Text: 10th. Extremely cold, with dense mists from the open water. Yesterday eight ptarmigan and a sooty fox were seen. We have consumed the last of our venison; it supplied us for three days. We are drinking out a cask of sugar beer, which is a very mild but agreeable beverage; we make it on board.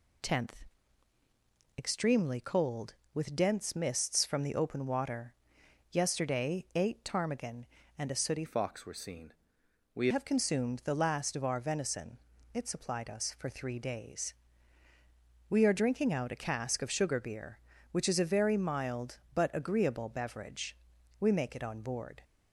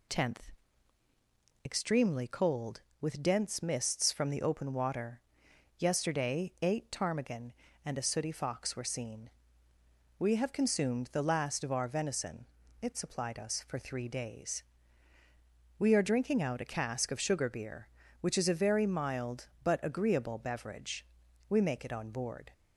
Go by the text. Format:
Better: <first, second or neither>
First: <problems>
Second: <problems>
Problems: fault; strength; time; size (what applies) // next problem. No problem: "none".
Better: second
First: changes voice from "fox" to "We"; from 8.4 to 10.0 s; 1.6 s long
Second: none